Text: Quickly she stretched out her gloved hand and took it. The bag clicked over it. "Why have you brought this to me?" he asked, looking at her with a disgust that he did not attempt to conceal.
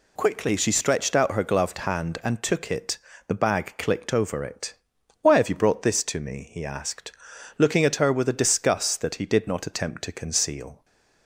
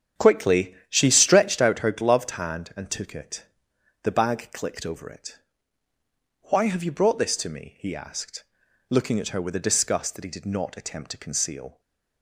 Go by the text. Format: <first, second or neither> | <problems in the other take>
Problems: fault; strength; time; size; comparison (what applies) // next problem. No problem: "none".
first | starts louder than the rest; strong; until 1.7 s; 8 dB // pauses between "Quickly" and "she"; slight; at 0.7 s; 0.16 s long // stays silent after the last word; slight; from 11.7 s on; 0.5 s long